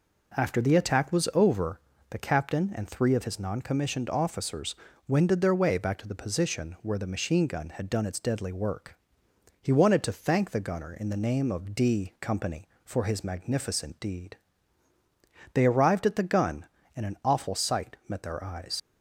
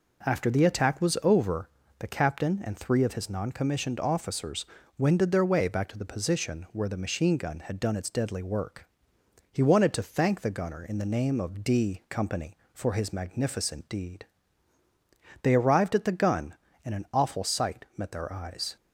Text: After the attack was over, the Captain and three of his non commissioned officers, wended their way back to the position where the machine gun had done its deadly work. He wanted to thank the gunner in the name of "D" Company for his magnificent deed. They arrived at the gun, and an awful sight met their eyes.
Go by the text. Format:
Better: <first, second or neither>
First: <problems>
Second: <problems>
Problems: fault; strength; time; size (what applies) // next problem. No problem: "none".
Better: second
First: leaves "eyes" unfinished; at 18.7 s; 70 ms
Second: none